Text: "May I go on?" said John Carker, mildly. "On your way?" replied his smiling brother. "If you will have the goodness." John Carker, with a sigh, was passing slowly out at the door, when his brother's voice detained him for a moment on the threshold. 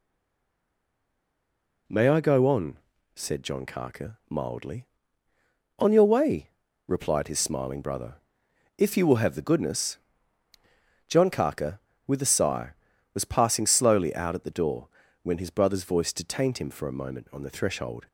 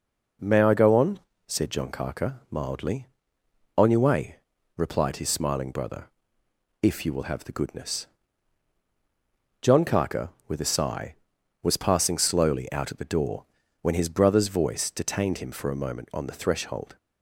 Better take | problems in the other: second | stays silent before the first word; noticeable; until 1.8 s; 1.8 s long

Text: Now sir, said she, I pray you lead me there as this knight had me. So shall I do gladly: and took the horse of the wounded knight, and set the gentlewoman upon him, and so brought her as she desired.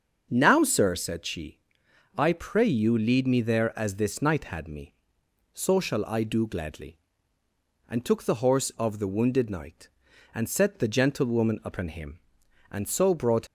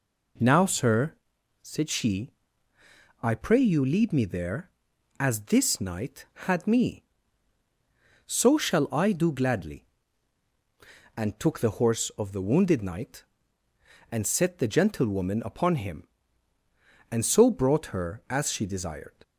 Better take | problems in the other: second | starts louder than the rest; until 1.3 s; 7 dB // stops before "her as she desired"; at 13.4 s

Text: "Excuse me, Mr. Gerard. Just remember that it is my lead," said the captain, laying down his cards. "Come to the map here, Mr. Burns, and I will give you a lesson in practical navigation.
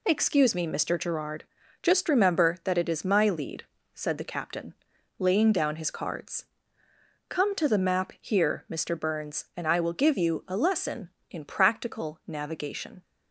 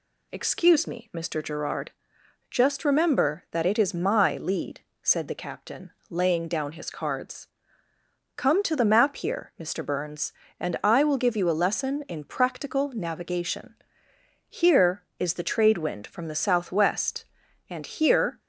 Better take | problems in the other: first | goes on to say "Here is the trade wind from the southwest and here"; strong; from 14.4 s on; 3.9 s long

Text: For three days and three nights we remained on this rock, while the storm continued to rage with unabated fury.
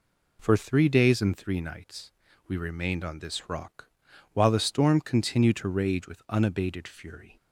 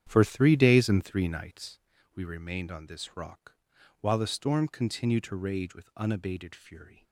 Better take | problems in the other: first | starts louder than the rest; strong; until 1.9 s; 9.5 dB // pauses between "nights" and "we"; slight; at 1.7 s; 0.36 s long; slight in the first

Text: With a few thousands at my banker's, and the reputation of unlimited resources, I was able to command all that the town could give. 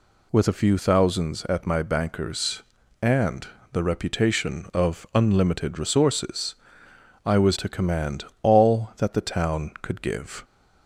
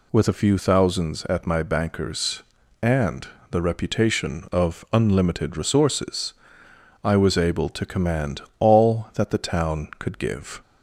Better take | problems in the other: second | pauses between "and" and "the"; slight; at 3.4 s; 0.24 s long; slight in the second // skips "able"; at 7.5 s // pauses between "command" and "all"; slight; at 8.2 s; 0.18 s long; slight in the second

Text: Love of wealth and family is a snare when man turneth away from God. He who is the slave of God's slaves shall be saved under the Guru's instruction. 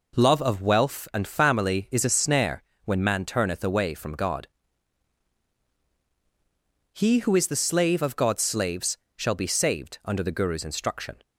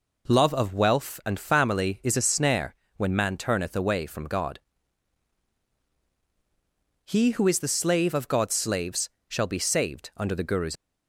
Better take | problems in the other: first | pauses between "snare" and "when"; slight; at 2.7 s; 0.22 s long; slight in the first // pauses between "slaves" and "shall"; slight; at 9.0 s; 0.20 s long; slight in the first // stops before "instruction"; at 10.7 s

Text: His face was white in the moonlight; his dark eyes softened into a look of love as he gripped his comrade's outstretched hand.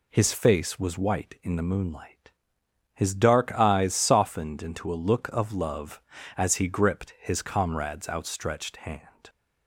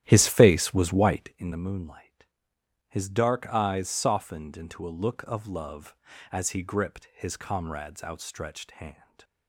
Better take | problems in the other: first | starts louder than the rest; strong; until 1.5 s; 11.5 dB

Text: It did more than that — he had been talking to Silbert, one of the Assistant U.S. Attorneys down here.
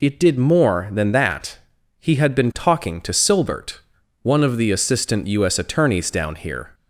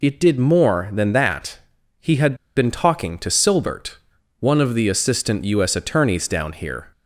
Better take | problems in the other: first | pauses between "had" and "been"; slight; at 2.3 s; 0.22 s long

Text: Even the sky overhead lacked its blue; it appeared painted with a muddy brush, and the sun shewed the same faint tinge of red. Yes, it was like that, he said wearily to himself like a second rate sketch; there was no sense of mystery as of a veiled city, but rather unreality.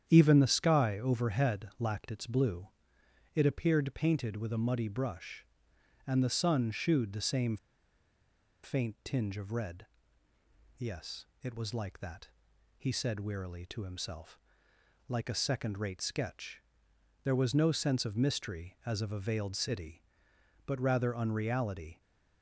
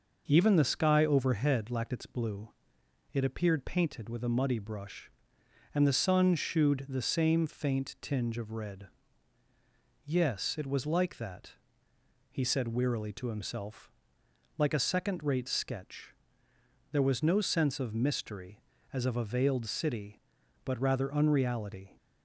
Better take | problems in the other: second | starts louder than the rest; strong; until 1.0 s; 9 dB // pauses between "same" and "faint"; at 7.5 s; 1.0 s long // pauses between "himself" and "like"; noticeable; at 14.3 s; 0.70 s long; noticeable in the second

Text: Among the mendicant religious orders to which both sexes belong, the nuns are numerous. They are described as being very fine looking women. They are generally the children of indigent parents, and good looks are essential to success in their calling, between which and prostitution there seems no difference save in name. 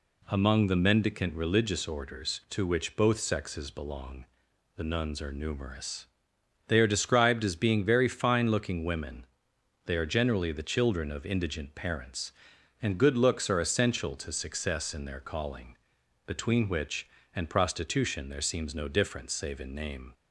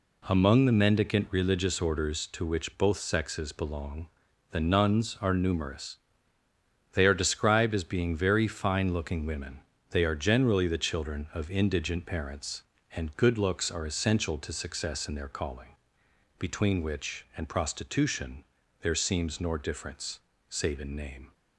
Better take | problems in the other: first | pauses between "prostitution" and "there"; slight; at 18.4 s; 0.34 s long // says "nor" for "no"; at 19.4 s // pauses between "difference" and "save"; slight; at 20.1 s; 0.28 s long

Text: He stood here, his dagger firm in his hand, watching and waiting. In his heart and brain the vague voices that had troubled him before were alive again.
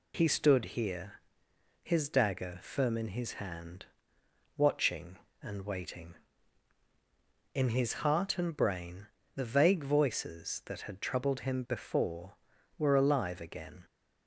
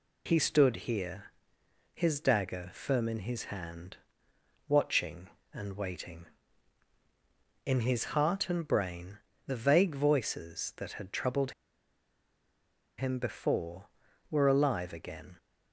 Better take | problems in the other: first | pauses between "brain" and "the"; slight; at 9.1 s; 0.28 s long; slight in the first // pauses between "troubled" and "him"; strong; at 11.5 s; 1.4 s long

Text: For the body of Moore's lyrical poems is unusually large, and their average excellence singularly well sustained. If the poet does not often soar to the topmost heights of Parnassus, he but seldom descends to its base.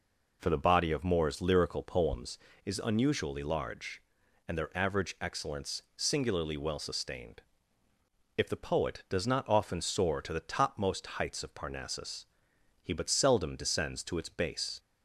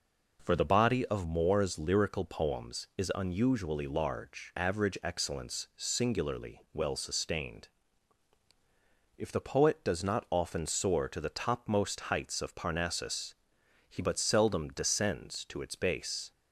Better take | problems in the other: first | skips "and their"; at 4.5 s

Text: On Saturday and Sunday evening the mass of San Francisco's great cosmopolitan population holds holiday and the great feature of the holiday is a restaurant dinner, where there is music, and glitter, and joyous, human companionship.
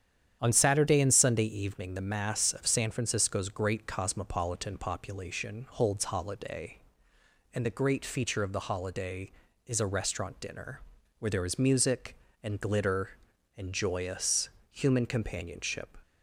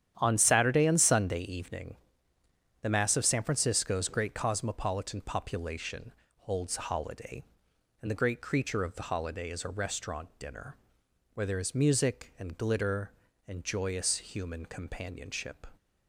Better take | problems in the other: first | starts louder than the rest; strong; until 1.1 s; 10 dB; strong in the first // pauses between "evening" and "the"; noticeable; at 1.9 s; 0.86 s long // pauses between "population" and "holds"; slight; at 6.1 s; 0.26 s long // says "creature" for "feature"; at 8.4 s

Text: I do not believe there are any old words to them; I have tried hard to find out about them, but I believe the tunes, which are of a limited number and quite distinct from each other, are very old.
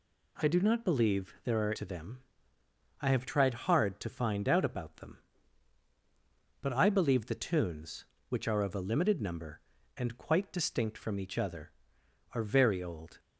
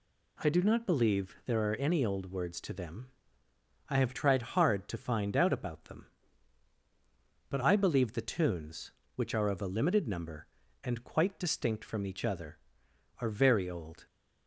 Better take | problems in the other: second | skips "any old words"; at 1.7 s

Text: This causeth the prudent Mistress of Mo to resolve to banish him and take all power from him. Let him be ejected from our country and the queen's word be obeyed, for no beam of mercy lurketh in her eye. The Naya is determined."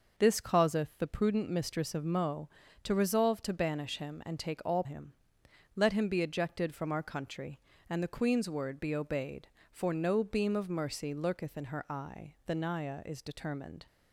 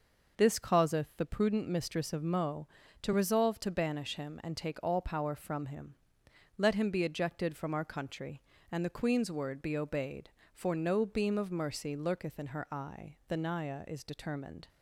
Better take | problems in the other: second | skips "power from"; at 4.8 s

